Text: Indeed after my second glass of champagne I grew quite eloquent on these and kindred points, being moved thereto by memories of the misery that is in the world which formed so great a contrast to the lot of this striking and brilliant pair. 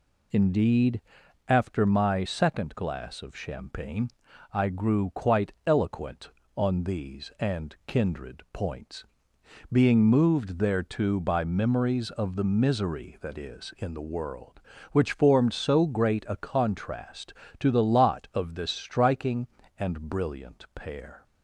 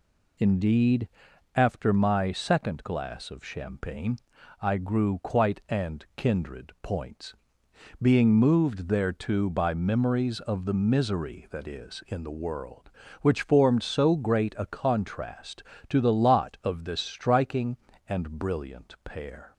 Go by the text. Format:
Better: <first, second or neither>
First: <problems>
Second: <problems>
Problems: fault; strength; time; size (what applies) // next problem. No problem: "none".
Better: first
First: pauses between "Indeed" and "after"; noticeable; at 1.0 s; 0.48 s long // pauses between "champagne" and "I"; at 4.0 s; 0.44 s long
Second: pauses between "Indeed" and "after"; noticeable; at 1.0 s; 0.48 s long // pauses between "champagne" and "I"; at 4.1 s; 0.44 s long // skips "eloquent on these"; at 5.6 s